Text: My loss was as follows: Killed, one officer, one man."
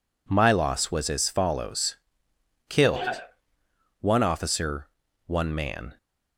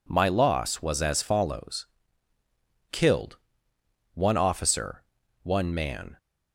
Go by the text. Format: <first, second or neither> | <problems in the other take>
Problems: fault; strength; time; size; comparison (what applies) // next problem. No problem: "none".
neither | none